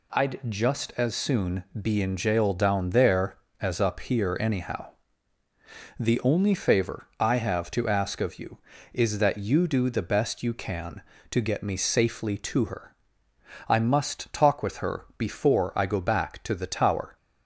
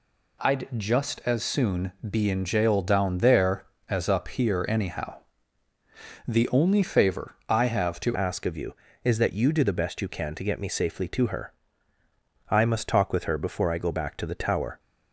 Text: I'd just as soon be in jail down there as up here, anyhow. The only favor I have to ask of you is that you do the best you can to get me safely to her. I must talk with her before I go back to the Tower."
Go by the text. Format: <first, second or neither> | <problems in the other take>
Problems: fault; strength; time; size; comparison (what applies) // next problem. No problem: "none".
first | pauses between "soon" and "be"; slight; at 1.9 s; 0.16 s long; slight in the first // changes voice at "ask"; from 8.1 s on; 6.6 s long